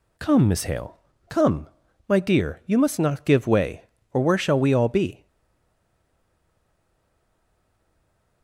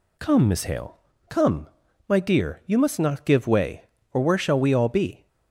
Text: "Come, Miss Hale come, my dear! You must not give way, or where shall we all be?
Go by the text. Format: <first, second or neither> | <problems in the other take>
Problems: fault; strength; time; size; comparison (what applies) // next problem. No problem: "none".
second | pauses between "Hale" and "come"; slight; at 0.9 s; 0.32 s long; slight in the second // stays silent after the last word; strong; from 5.2 s on; 3.2 s long